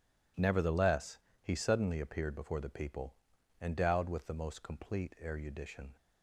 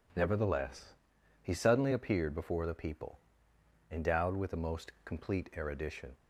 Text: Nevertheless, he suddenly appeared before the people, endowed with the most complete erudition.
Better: neither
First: none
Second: none

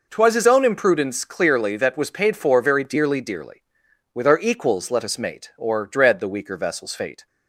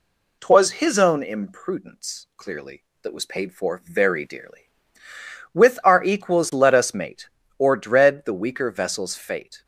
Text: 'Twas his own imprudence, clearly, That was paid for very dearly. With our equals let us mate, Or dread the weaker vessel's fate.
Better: second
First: says "dearly" twice; at 3.2 s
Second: none

